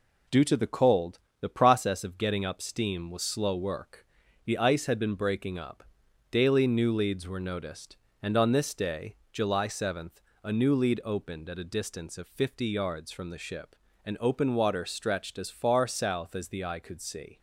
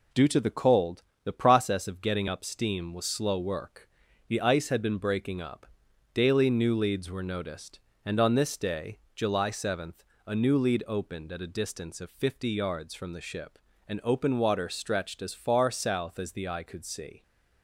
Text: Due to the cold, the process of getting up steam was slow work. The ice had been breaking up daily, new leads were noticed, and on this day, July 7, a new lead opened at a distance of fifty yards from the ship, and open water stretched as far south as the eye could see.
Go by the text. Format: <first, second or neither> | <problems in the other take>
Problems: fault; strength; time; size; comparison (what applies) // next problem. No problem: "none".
neither | pauses between "up" and "daily"; noticeable; the same in both